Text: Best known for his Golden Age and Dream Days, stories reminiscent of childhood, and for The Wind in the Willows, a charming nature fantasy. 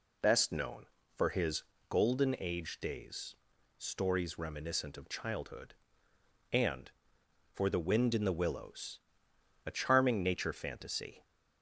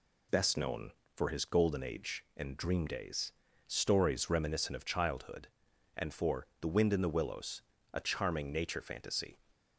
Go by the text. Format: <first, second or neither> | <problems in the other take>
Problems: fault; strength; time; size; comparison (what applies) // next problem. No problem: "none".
second | pauses between "his" and "Golden"; slight; at 1.6 s; 0.26 s long // skips "and Dream"; at 2.7 s